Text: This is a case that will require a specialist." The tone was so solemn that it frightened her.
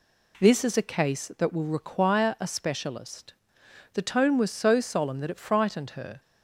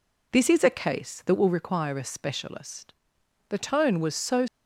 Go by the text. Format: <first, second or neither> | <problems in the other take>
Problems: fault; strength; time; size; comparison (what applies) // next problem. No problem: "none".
first | stops before "solemn that it frightened her"; at 4.4 s